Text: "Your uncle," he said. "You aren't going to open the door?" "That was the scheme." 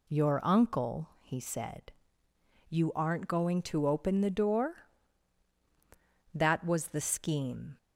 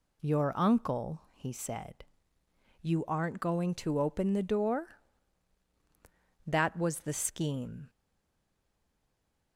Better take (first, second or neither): first